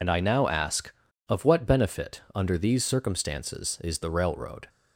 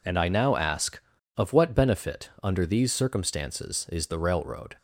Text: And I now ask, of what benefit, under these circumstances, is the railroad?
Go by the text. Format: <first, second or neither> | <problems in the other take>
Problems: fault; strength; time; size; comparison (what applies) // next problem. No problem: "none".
second | loses the start of "And"; at 0.0 s; 45 ms